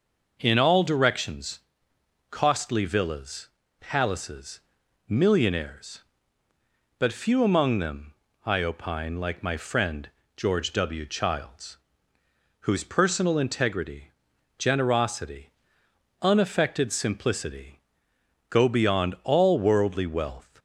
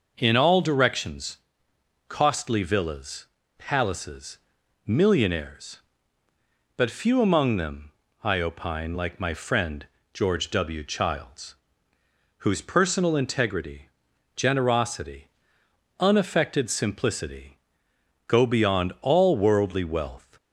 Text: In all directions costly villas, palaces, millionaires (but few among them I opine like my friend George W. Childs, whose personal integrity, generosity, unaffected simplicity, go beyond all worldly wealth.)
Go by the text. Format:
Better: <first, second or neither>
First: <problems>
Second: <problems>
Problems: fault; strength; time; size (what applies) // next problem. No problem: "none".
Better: neither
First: pauses between "directions" and "costly"; noticeable; at 1.6 s; 0.68 s long // pauses between "them" and "I"; slight; at 8.1 s; 0.32 s long // pauses between "friend" and "George"; slight; at 10.1 s; 0.26 s long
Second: pauses between "directions" and "costly"; noticeable; at 1.3 s; 0.68 s long // pauses between "them" and "I"; slight; at 7.9 s; 0.32 s long // pauses between "friend" and "George"; slight; at 9.8 s; 0.26 s long